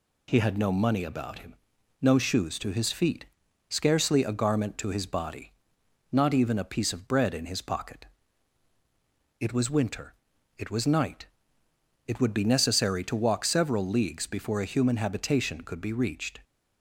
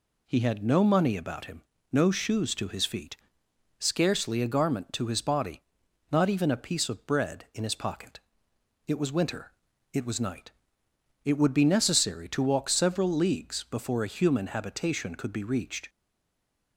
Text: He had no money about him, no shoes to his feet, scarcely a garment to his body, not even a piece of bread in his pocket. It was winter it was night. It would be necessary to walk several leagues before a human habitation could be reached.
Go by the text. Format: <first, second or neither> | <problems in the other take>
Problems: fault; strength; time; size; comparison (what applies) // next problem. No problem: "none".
first | pauses between "winter" and "it"; at 9.5 s; 0.40 s long; noticeable in the first // stays silent after the last word; slight; from 15.8 s on; 0.9 s long